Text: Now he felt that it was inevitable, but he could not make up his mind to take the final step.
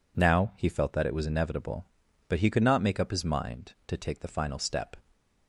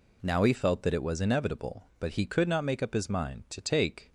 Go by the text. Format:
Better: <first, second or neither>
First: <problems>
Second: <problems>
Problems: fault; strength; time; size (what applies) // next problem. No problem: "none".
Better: first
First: none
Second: stops before "the final step"; at 4.0 s